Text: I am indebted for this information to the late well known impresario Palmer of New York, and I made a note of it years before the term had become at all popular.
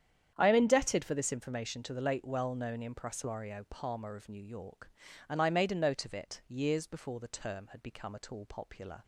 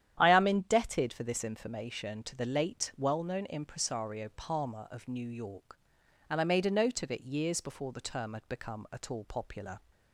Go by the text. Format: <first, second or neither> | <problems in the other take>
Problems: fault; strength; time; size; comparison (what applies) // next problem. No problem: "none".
neither | starts louder than the rest; strong; the same in both